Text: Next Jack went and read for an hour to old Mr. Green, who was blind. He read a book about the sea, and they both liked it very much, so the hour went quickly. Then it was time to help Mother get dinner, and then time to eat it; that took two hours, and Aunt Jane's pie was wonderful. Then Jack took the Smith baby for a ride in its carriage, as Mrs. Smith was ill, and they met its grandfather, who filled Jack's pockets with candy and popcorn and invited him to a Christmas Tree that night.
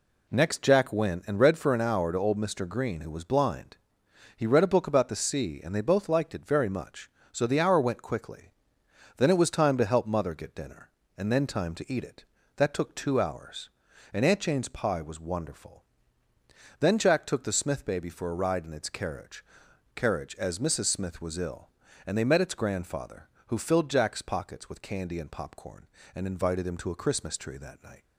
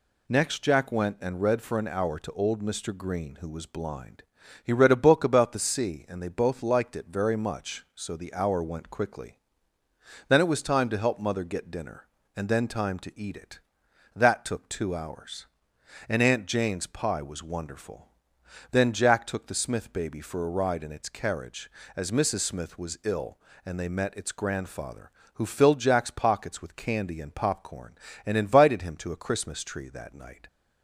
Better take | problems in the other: second | says "carriage" twice; at 19.9 s

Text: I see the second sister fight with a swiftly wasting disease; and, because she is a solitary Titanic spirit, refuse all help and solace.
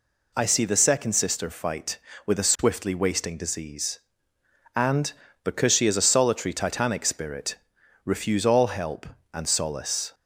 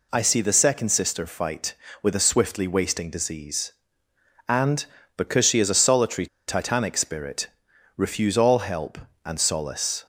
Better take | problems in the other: first | pauses between "solitary" and "Titanic"; slight; at 6.2 s; 0.20 s long

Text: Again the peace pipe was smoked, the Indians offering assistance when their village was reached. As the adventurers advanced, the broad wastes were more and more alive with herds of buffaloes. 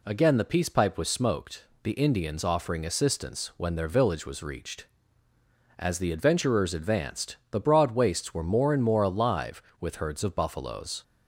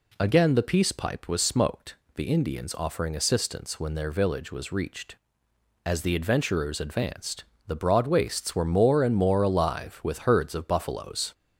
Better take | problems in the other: neither | none

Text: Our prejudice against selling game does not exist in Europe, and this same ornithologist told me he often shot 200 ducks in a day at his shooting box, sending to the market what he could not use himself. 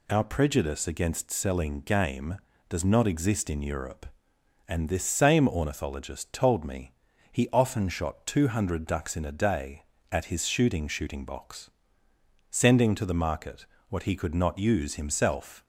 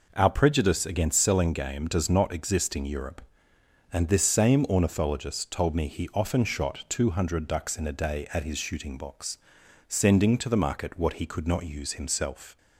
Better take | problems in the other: second | pauses between "me" and "he"; at 6.9 s; 0.40 s long // says "shooting" twice; at 10.8 s // pauses between "market" and "what"; slight; at 13.6 s; 0.24 s long

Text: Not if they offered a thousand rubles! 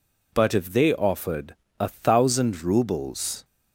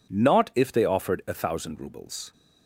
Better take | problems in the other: second | says "But" for "Not"; at 0.3 s // pauses between "offered" and "a"; slight; at 1.5 s; 0.24 s long

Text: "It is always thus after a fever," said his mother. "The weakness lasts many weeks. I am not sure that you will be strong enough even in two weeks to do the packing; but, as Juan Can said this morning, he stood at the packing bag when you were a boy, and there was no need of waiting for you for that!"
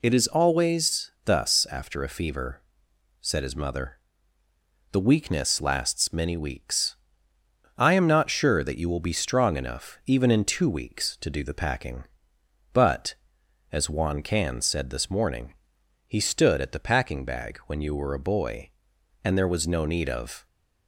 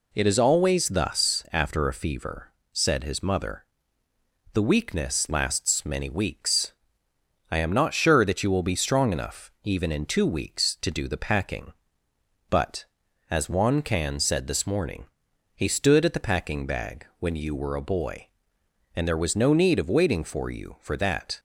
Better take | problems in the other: second | stops before "waiting for you for that"; at 20.4 s

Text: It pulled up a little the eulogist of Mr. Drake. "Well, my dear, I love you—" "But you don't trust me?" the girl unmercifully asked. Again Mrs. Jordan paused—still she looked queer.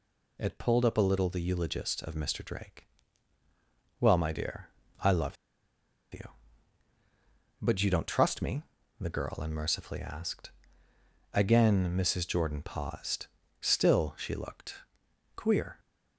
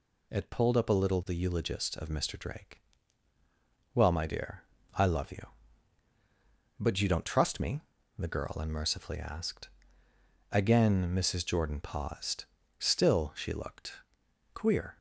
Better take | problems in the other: second | pauses between "love" and "you"; noticeable; at 5.3 s; 0.77 s long // pauses between "looked" and "queer"; noticeable; at 14.7 s; 0.58 s long; noticeable in the second

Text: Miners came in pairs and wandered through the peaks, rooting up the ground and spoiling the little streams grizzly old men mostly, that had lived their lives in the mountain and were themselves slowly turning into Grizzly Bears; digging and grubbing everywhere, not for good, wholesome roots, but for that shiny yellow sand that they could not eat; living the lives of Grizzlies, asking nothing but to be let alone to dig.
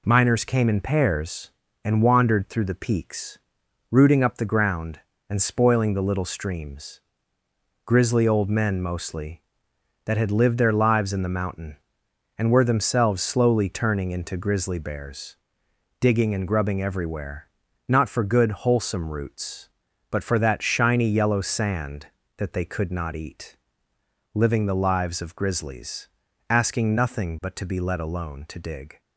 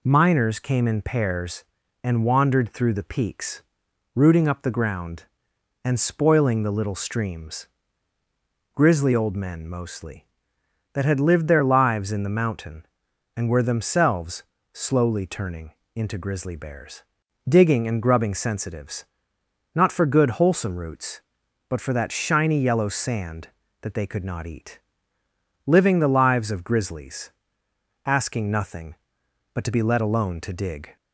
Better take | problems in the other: first | pauses between "streams" and "grizzly"; at 7.6 s; 1.0 s long; noticeable in the first // pauses between "themselves" and "slowly"; slight; at 14.4 s; 0.28 s long // pauses between "turning" and "into"; slight; at 15.7 s; 0.20 s long // says "sensitives" for "everywhere"; at 18.3 s

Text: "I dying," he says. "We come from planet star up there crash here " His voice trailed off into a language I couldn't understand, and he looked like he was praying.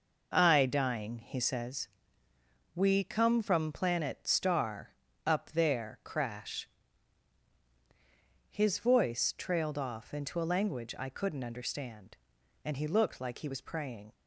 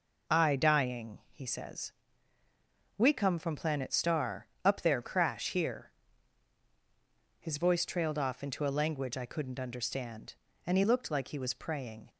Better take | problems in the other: second | pauses between "star" and "up"; slight; at 4.9 s; 0.32 s long; slight in the second // skips "here"; at 7.1 s

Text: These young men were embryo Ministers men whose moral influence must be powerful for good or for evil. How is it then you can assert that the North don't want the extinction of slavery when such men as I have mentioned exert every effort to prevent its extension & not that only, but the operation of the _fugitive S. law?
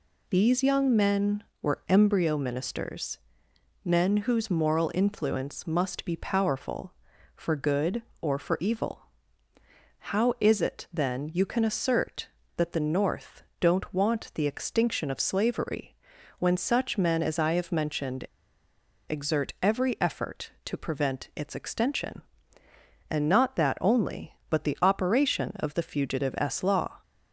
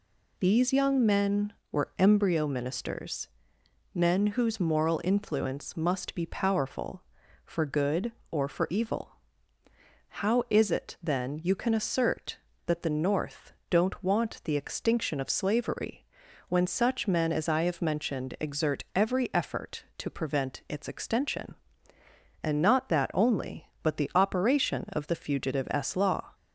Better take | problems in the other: second | pauses between "Ministers" and "men"; noticeable; at 3.1 s; 0.66 s long; noticeable in the second // pauses between "North" and "don't"; slight; at 13.4 s; 0.18 s long; slight in the second // pauses between "slavery" and "when"; at 15.9 s; 0.44 s long; also in the second // pauses between "mentioned" and "exert"; noticeable; at 18.2 s; 0.80 s long

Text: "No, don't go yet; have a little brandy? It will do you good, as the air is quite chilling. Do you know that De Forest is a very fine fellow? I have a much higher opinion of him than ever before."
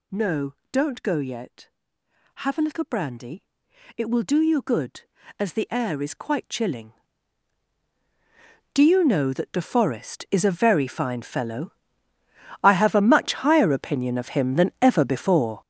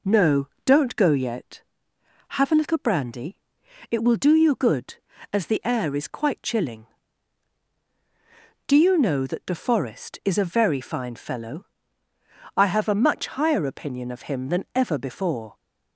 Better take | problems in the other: second | gets louder; strong; throughout; 11.5 dB

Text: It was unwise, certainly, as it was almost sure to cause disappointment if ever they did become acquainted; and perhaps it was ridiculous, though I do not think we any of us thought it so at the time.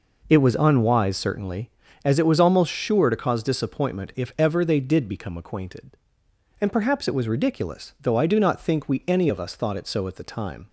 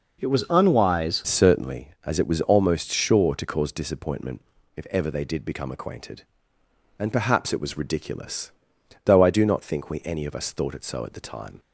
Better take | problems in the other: first | changes voice at "certainly"; from 1.2 s on; 10.3 s long // pauses between "disappointment" and "if"; slight; at 4.4 s; 0.36 s long

